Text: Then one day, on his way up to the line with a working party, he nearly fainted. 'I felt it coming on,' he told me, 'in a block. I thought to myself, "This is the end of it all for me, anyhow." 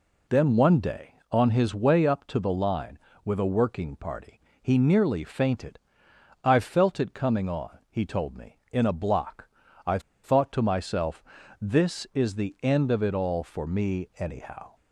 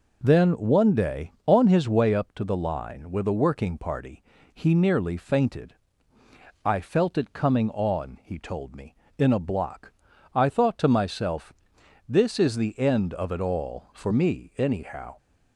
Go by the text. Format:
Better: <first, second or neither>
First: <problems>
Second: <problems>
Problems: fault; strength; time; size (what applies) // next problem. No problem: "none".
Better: second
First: pauses between "I" and "thought"; slight; at 9.9 s; 0.24 s long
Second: none